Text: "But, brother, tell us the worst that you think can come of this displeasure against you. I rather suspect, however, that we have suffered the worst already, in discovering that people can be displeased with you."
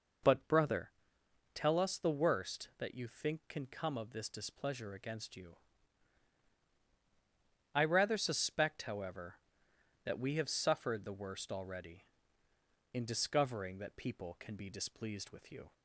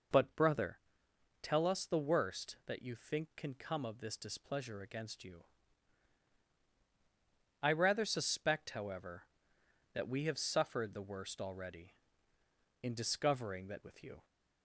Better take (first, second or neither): first